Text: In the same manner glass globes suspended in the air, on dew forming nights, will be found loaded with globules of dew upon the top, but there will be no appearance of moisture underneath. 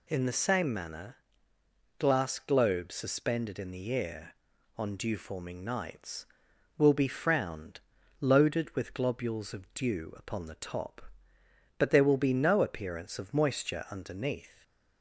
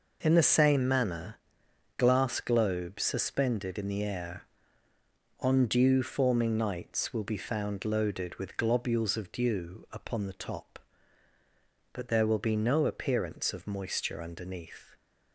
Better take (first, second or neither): second